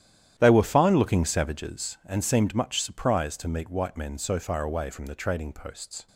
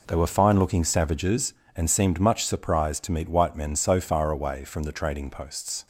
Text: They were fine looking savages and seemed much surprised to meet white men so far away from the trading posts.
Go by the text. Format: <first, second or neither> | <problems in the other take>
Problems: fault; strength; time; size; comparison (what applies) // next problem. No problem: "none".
second | starts louder than the rest; strong; until 2.1 s; 11 dB